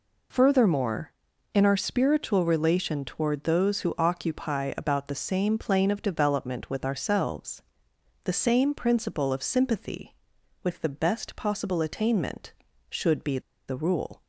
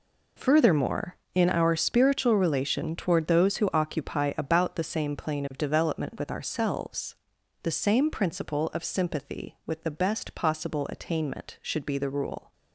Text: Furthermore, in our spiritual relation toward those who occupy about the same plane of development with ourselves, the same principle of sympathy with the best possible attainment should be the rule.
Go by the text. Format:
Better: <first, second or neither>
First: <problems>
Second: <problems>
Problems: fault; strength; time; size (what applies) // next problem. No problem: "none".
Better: second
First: pauses between "be" and "the"; slight; at 13.3 s; 0.28 s long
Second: none